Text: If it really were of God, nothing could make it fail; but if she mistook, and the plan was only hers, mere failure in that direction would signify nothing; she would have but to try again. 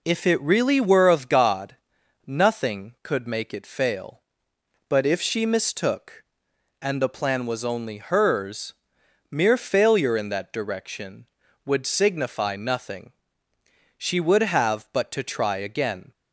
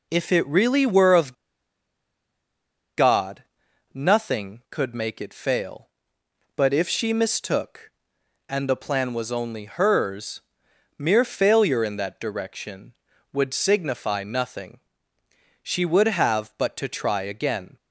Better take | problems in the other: first | pauses between "of" and "God"; strong; at 1.3 s; 1.6 s long

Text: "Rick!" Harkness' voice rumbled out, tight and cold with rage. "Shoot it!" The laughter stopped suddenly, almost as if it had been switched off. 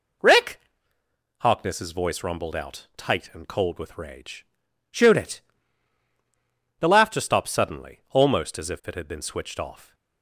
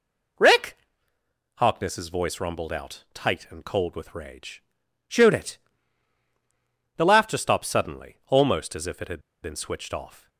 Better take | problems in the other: first | pauses between "had" and "been"; slight; at 9.1 s; 0.22 s long

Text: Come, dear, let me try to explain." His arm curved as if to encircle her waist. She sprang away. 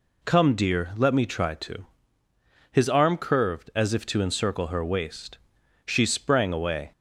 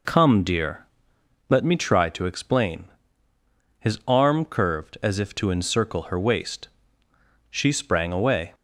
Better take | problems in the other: second | skips "explain"; at 2.2 s

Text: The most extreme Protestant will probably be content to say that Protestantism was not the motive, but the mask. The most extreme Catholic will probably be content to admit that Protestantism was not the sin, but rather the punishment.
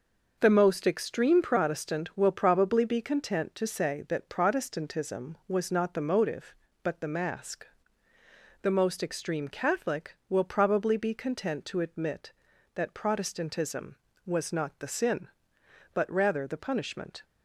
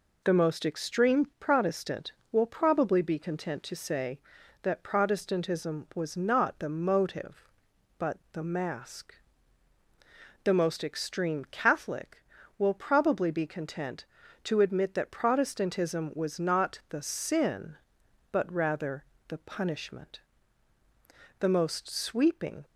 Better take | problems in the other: first | pauses between "rather" and "the"; slight; at 19.0 s; 0.24 s long // goes on to say "The most sweeping"; noticeable; from 21.4 s on; 1.2 s long

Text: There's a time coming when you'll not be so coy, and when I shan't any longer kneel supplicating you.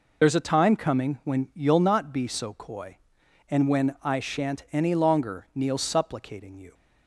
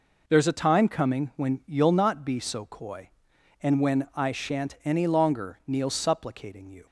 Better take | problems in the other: second | loses the start of "There's"; at 0.2 s; 60 ms

